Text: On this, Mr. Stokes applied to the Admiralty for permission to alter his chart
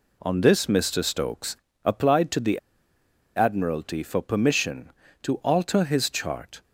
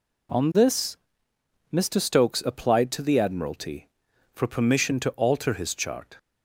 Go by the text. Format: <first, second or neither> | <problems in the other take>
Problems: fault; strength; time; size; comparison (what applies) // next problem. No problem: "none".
second | pauses between "Stokes" and "applied"; slight; at 1.5 s; 0.26 s long // pauses between "the" and "Admiralty"; noticeable; at 2.5 s; 0.78 s long